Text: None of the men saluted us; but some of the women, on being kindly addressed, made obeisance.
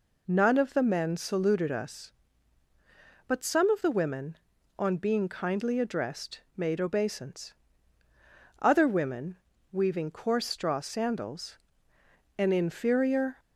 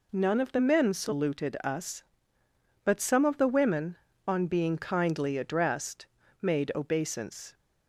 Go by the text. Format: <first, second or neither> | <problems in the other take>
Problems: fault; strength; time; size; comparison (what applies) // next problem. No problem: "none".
second | goes on to say "Other women weaving coarse straw sandals an inferior"; strong; from 8.6 s on; 4.7 s long